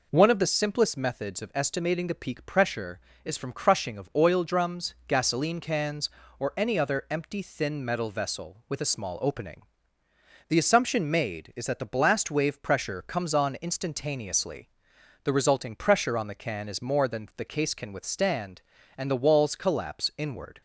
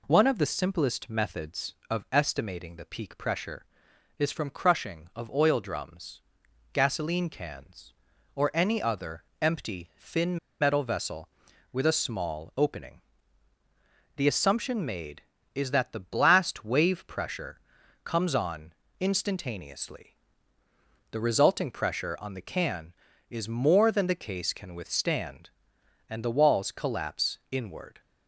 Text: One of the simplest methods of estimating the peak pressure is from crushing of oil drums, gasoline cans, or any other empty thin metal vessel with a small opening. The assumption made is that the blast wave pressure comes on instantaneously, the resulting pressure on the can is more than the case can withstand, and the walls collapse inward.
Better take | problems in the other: first | pauses between "other" and "empty"; slight; at 9.2 s; 0.18 s long // pauses between "thin" and "metal"; slight; at 10.3 s; 0.24 s long // pauses between "pressure" and "comes"; at 17.6 s; 0.42 s long // pauses between "on" and "instantaneously"; slight; at 18.7 s; 0.26 s long

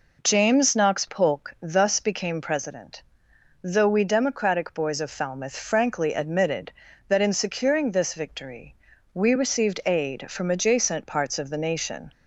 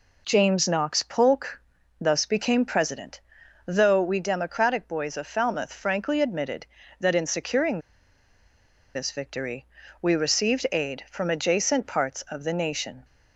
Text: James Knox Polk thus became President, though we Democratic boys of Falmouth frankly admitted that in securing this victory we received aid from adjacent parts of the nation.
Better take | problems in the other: first | pauses between "Polk" and "thus"; at 1.6 s; 0.40 s long // pauses between "securing" and "this"; at 7.7 s; 1.1 s long // pauses between "victory" and "we"; at 9.6 s; 0.38 s long; also in the first

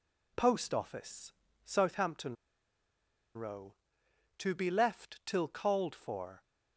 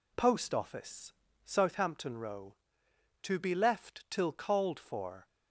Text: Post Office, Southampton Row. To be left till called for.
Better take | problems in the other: second | pauses between "Southampton" and "Row"; at 2.3 s; 1.0 s long

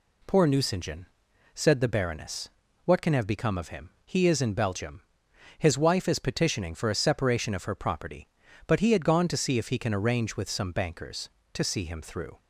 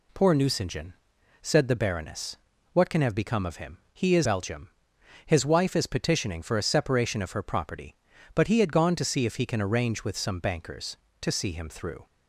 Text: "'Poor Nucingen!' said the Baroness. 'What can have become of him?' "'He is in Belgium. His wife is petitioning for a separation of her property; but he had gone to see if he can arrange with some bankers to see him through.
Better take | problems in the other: first | skips "in"; at 4.2 s

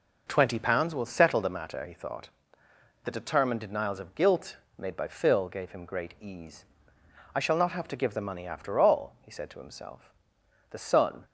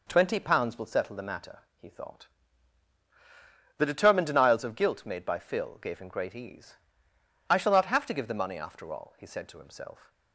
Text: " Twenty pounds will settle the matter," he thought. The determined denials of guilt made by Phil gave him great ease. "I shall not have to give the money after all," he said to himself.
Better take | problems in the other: second | pauses between "guilt" and "made"; slight; at 4.5 s; 0.20 s long // goes on to say "The son"; from 10.6 s on; 0.54 s long

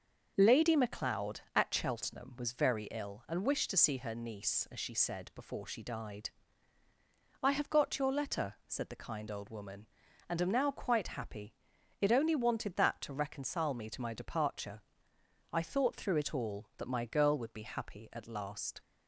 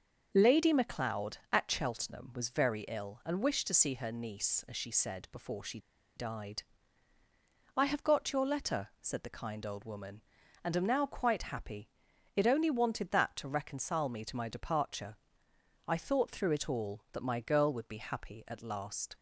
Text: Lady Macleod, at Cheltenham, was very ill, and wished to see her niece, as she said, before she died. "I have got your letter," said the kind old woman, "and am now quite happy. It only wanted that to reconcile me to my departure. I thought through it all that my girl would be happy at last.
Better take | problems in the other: first | starts louder than the rest; until 1.3 s; 6.5 dB; also in the first // pauses between "she" and "died"; at 5.7 s; 0.38 s long

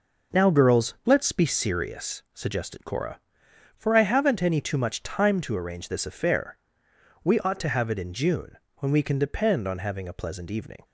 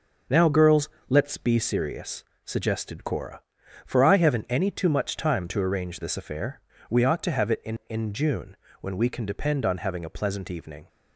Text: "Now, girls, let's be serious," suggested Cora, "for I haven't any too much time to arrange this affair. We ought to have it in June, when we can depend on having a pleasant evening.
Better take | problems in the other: first | says "in" twice; at 7.8 s

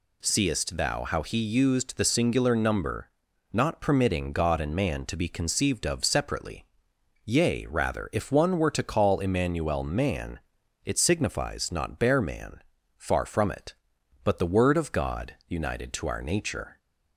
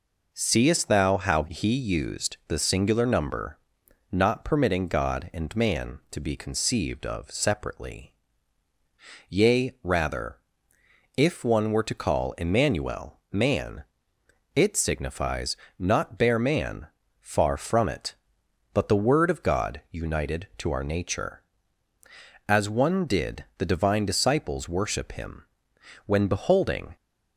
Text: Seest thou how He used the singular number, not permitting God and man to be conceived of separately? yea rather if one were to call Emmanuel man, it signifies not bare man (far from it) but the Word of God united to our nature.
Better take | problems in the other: first | pauses between "rather" and "if"; noticeable; at 10.3 s; 0.80 s long // pauses between "signifies" and "not"; slight; at 15.5 s; 0.24 s long // goes on to say "As One did the Divine disciples worship Him when beholding"; strong; from 22.4 s on; 4.4 s long

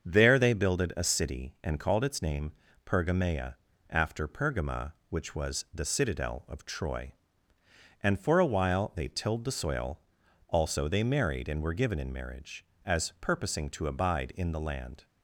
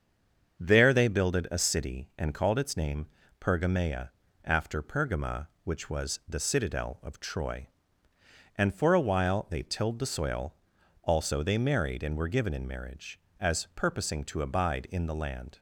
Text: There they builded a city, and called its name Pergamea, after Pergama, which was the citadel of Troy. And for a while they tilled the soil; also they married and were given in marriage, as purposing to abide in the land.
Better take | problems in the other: first | stays silent before the first word; slight; until 0.5 s; 0.5 s long // starts louder than the rest; until 1.6 s; 7 dB; also in the first // pauses between "name" and "Pergamea"; slight; at 3.0 s; 0.34 s long; slight in the first

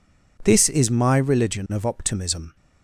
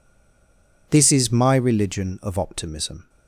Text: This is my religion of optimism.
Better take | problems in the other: first | stays silent before the first word; slight; until 0.8 s; 0.8 s long

